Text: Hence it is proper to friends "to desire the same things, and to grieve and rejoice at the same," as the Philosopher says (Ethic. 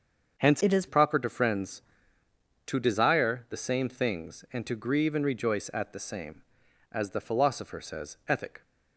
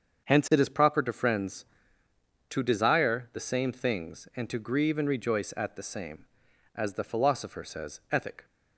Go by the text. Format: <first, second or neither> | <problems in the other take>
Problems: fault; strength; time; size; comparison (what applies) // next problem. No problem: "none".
second | starts louder than the rest; until 1.4 s; 6.5 dB; also in the second // changes voice from "it" to "is"; from 0.6 to 0.8 s; 0.2 s long